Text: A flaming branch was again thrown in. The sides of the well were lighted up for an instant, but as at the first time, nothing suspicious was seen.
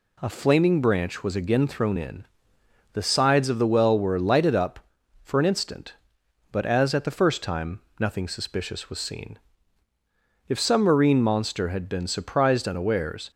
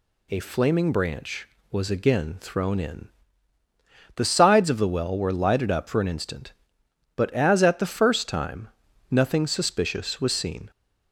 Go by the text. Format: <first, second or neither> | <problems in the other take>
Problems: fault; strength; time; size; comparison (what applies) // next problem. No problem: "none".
second | goes on to say "If some marine monster had been surprised unawares"; strong; from 10.4 s on; 2.8 s long